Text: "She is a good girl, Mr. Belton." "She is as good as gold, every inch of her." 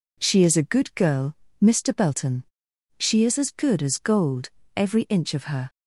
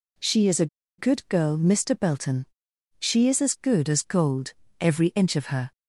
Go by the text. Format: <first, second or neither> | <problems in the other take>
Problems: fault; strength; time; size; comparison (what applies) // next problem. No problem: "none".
first | pauses between "a" and "good"; slight; at 0.6 s; 0.32 s long